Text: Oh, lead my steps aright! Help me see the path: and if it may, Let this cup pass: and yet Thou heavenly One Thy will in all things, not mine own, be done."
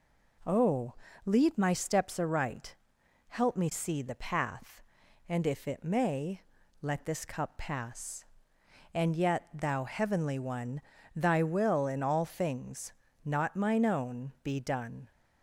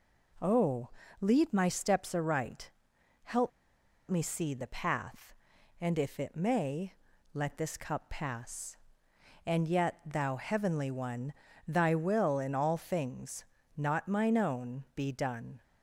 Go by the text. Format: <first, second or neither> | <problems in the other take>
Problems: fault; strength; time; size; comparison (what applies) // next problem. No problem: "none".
first | pauses between "Help" and "me"; noticeable; at 3.5 s; 0.58 s long // pauses between "One" and "Thy"; slight; at 11.3 s; 0.34 s long; slight in the first